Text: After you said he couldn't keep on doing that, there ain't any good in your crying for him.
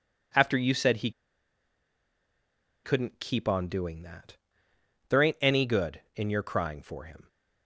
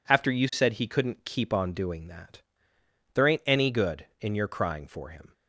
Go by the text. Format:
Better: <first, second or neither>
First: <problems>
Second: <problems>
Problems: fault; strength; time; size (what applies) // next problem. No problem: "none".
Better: second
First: pauses between "he" and "couldn't"; strong; at 1.1 s; 1.7 s long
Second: none